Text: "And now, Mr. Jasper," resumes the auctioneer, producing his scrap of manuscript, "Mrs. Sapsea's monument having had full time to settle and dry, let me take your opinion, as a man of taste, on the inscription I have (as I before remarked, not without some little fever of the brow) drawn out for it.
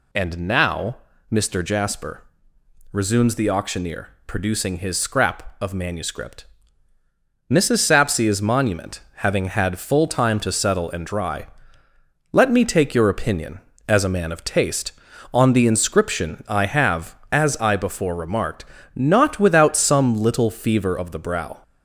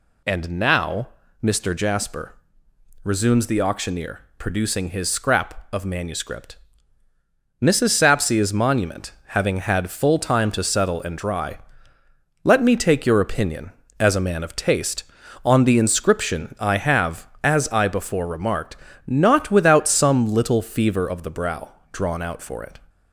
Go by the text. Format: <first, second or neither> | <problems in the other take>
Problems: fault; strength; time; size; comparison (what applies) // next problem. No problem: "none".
second | pauses between "monument" and "having"; slight; at 9.0 s; 0.16 s long; slight in the second // stops before "drawn out for it"; at 21.6 s